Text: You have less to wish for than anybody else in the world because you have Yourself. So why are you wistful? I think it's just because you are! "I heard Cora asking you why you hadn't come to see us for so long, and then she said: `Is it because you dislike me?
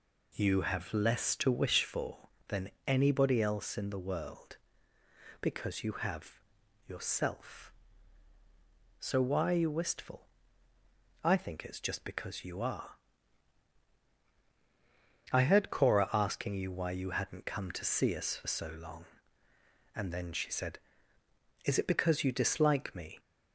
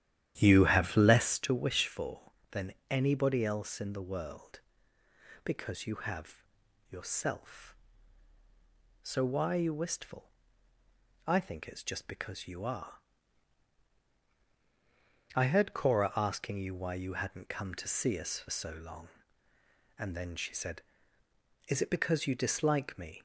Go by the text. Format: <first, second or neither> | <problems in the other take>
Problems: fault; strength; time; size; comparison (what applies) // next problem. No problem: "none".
first | starts louder than the rest; strong; until 1.3 s; 11.5 dB // pauses between "than" and "anybody"; slight; at 2.7 s; 0.16 s long; slight in the first // pauses between "have" and "Yourself"; noticeable; at 6.4 s; 0.46 s long; noticeable in the first